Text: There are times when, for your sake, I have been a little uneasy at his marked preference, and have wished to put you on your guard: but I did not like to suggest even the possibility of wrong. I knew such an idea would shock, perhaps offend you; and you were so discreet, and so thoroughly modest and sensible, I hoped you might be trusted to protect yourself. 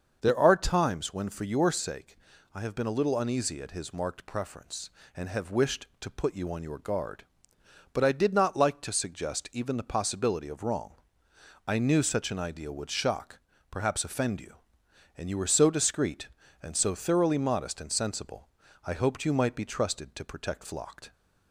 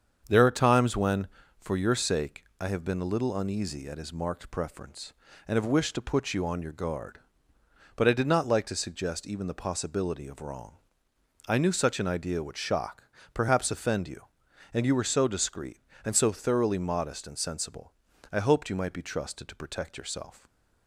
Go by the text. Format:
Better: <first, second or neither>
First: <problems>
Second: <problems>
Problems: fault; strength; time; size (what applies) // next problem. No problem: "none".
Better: second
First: starts louder than the rest; until 1.2 s; 6.5 dB // says "flocked" for "yourself"; at 20.6 s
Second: starts louder than the rest; strong; until 1.6 s; 7 dB